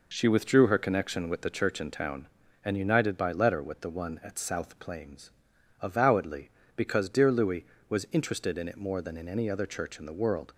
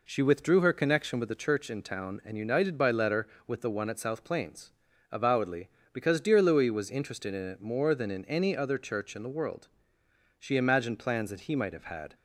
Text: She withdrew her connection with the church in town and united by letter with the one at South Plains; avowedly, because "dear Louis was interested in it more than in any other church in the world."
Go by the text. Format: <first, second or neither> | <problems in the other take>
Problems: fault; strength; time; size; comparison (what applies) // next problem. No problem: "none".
first | goes on to say "She imagined plans that he might have had"; strong; from 10.3 s on; 1.7 s long